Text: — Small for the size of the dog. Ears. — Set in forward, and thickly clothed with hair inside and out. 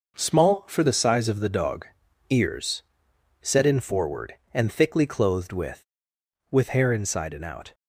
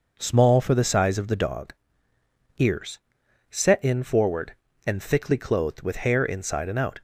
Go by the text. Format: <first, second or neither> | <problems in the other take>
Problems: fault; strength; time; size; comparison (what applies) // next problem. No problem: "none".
second | says "with" twice; at 6.5 s